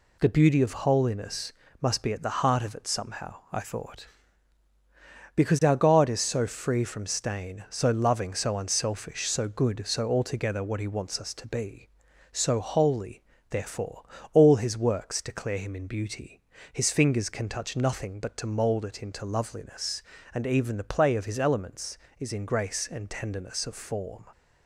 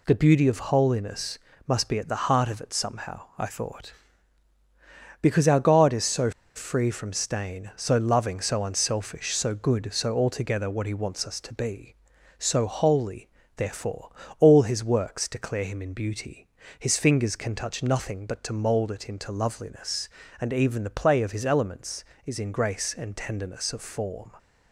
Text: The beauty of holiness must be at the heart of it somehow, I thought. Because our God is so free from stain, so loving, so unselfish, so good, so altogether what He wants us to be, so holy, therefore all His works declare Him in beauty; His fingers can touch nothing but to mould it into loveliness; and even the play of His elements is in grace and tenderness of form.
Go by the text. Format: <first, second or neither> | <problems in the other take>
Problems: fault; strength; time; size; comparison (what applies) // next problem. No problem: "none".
first | pauses between "holiness" and "must"; slight; at 1.3 s; 0.28 s long; slight in the first // pauses between "so" and "free"; slight; at 6.3 s; 0.25 s long // pauses between "therefore" and "all"; slight; at 14.0 s; 0.32 s long; slight in the first